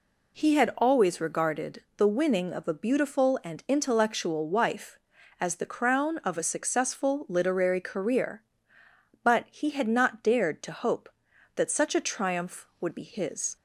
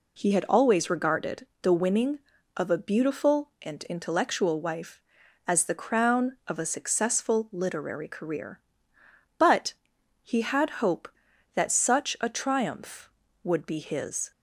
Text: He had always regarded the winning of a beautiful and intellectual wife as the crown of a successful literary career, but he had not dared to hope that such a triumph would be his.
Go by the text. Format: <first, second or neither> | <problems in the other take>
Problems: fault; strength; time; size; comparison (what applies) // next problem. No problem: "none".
first | pauses between "regarded" and "the"; slight; at 1.4 s; 0.16 s long // pauses between "but" and "he"; noticeable; at 9.7 s; 0.48 s long // skips "not dared to"; at 10.8 s